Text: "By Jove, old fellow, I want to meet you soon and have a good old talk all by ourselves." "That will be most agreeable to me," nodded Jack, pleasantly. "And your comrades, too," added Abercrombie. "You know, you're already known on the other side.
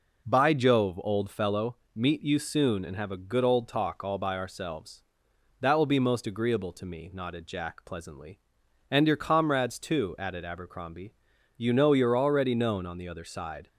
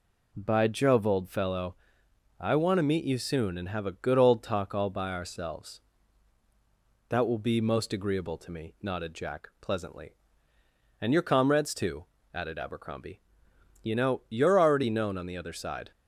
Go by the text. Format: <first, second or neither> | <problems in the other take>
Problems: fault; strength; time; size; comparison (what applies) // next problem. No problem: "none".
second | skips "I want to"; at 1.8 s